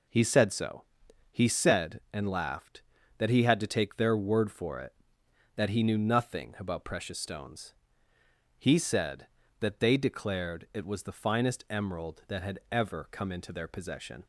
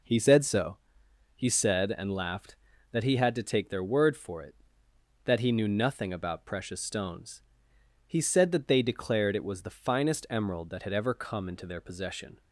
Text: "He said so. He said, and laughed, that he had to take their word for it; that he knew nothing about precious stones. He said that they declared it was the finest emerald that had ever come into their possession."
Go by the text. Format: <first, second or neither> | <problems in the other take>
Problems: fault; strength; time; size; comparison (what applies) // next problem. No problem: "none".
neither | none